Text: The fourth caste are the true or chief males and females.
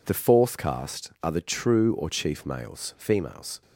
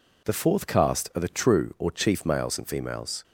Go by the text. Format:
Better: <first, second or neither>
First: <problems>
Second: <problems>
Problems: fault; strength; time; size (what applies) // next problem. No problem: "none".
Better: second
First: skips "and"; at 2.9 s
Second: none